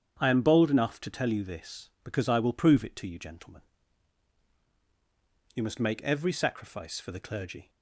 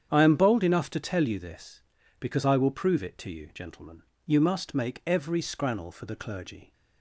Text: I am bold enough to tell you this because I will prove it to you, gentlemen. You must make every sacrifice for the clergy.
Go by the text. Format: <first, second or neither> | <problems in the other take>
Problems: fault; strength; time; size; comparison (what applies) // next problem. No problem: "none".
first | starts louder than the rest; strong; until 1.1 s; 8.5 dB; strong in the first // says "scrannel" for "sacrifice"; at 5.4 s